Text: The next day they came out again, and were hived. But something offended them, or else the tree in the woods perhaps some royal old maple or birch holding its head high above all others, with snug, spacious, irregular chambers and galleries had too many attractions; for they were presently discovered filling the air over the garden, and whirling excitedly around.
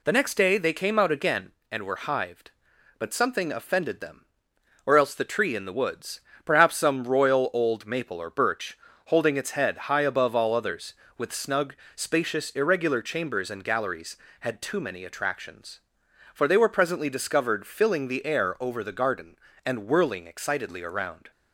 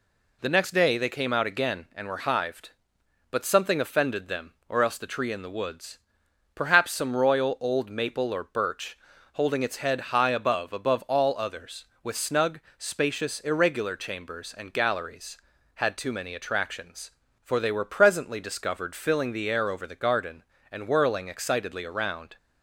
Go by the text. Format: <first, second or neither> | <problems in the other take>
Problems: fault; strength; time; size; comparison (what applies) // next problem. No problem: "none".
first | pauses between "woods" and "perhaps"; noticeable; at 5.9 s; 0.56 s long; slight in the first // pauses between "birch" and "holding"; slight; at 8.9 s; 0.36 s long; slight in the first // says "above" twice; at 10.7 s